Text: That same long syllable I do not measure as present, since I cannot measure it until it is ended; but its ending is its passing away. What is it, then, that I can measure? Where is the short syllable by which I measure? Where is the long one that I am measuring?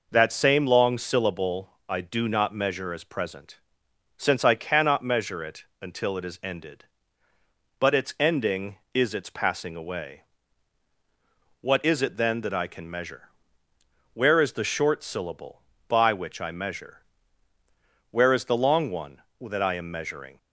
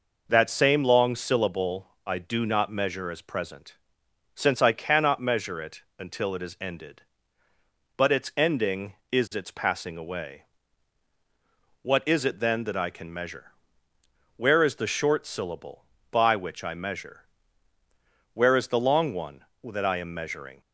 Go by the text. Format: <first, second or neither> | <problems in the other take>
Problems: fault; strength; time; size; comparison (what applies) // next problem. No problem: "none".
neither | pauses between "syllable" and "I"; slight; the same in both // pauses between "it" and "until"; slight; the same in both